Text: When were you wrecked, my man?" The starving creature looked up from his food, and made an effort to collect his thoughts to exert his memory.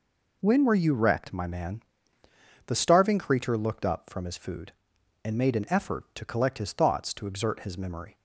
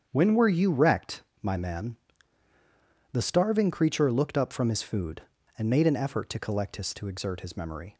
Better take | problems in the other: first | starts louder than the rest; strong; until 1.1 s; 8 dB // skips "thoughts"; at 6.9 s

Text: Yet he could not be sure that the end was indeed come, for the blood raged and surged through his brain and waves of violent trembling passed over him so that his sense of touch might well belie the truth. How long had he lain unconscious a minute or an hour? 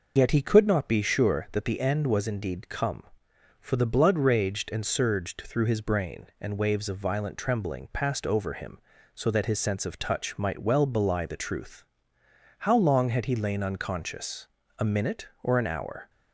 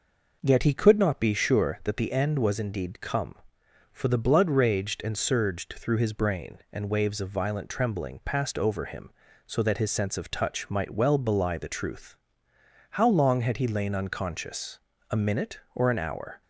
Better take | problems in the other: second | loses the start of "Yet"; at 0.1 s; 65 ms // pauses between "unconscious" and "a"; slight; at 14.4 s; 0.30 s long; slight in the second

